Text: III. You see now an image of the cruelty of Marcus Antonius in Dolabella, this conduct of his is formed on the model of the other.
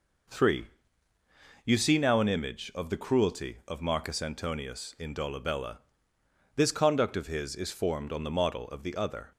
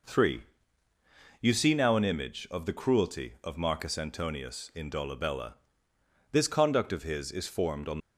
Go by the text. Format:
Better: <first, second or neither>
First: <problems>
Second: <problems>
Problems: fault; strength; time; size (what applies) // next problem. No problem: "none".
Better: first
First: none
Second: stops before "the model of the other"; at 7.9 s